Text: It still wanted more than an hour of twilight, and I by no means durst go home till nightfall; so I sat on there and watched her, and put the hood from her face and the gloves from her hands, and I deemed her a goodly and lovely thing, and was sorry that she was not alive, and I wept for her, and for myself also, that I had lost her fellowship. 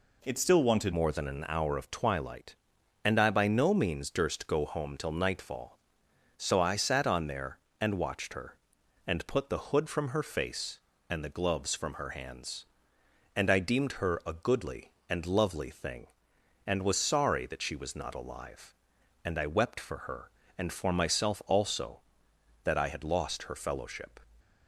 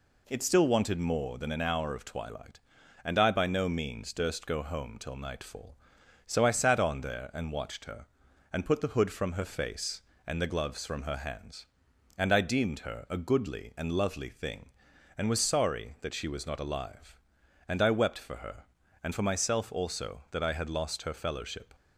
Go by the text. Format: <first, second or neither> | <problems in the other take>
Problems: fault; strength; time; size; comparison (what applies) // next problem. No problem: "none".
second | changes voice at "more"; from 0.9 s on; 23.2 s long